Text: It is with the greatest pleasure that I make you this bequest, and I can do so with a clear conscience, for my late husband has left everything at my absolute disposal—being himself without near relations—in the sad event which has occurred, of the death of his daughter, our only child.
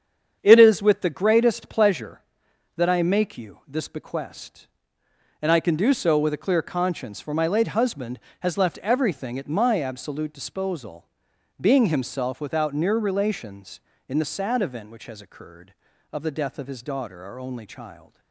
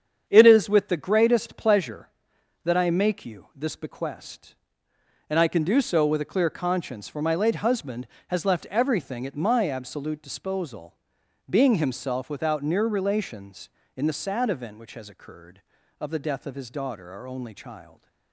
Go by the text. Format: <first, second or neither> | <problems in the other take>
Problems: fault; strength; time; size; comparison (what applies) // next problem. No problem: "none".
neither | starts louder than the rest; strong; the same in both